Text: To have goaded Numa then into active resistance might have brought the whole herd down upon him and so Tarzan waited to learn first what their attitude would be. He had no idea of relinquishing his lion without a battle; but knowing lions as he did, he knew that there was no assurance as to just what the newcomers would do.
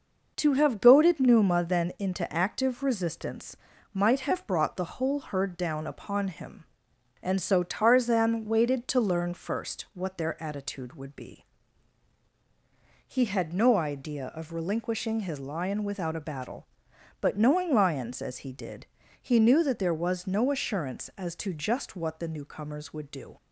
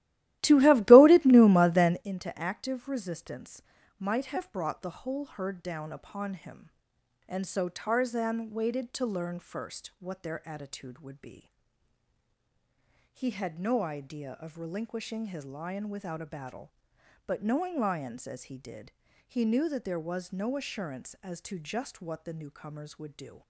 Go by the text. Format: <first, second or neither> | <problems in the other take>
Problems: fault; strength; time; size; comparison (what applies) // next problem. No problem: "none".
first | starts louder than the rest; strong; until 2.1 s; 15.5 dB // pauses between "resistance" and "might"; slight; at 3.6 s; 0.36 s long; slight in the first